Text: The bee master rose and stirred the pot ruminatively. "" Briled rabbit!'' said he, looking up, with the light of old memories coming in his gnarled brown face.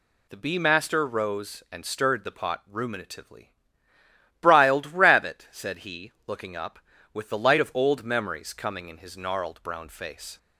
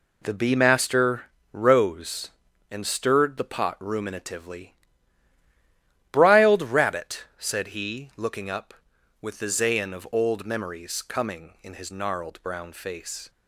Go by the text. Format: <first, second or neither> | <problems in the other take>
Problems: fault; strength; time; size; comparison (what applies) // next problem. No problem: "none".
first | pauses between "master" and "rose"; slight; at 1.2 s; 0.30 s long // says "zayin" for "light"; at 9.4 s